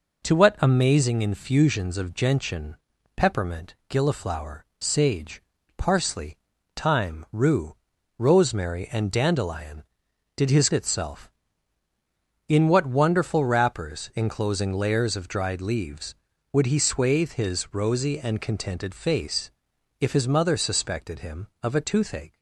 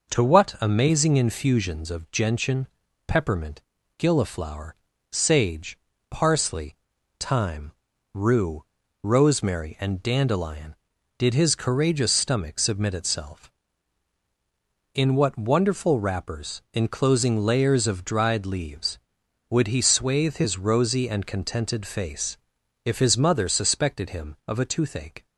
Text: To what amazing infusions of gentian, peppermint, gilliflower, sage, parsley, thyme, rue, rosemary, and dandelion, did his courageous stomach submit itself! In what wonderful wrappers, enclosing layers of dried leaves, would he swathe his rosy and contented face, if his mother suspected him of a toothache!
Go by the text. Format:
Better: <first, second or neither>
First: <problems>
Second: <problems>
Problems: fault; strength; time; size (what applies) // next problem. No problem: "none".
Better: second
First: skips "courageous stomach submit"; at 10.7 s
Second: none